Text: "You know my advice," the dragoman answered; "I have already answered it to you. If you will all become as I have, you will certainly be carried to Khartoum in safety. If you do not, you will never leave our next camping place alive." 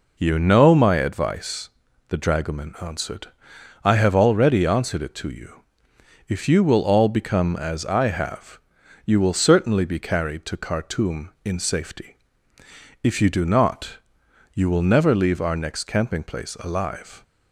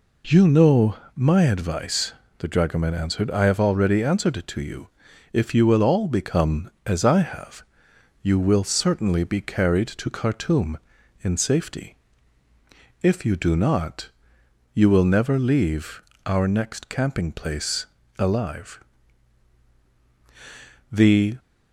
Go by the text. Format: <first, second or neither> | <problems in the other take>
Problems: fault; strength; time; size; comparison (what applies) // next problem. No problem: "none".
first | pauses between "know" and "my"; slight; at 0.9 s; 0.20 s long // pauses between "leave" and "our"; slight; at 16.0 s; 0.24 s long // pauses between "place" and "alive"; slight; at 17.8 s; 0.32 s long // goes on to say "The"; slight; from 20.8 s on; 0.46 s long